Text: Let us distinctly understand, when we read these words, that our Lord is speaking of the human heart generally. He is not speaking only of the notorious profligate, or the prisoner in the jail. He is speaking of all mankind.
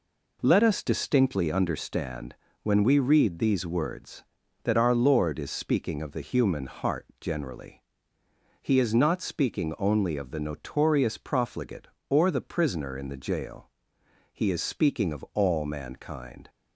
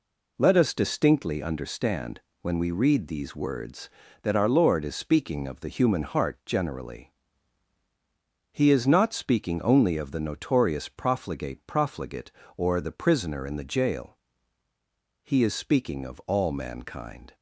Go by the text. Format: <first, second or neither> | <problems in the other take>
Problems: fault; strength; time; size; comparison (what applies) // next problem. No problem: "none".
first | says "profligate" twice; at 11.6 s